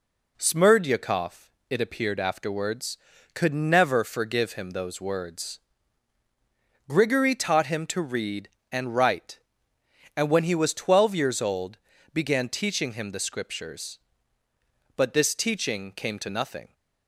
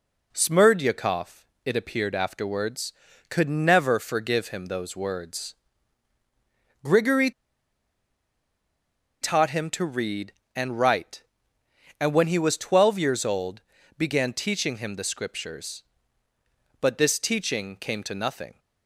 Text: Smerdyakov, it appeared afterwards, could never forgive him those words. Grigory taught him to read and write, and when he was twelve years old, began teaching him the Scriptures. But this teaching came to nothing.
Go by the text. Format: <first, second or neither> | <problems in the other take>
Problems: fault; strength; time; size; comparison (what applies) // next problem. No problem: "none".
first | pauses between "Grigory" and "taught"; strong; at 7.3 s; 1.9 s long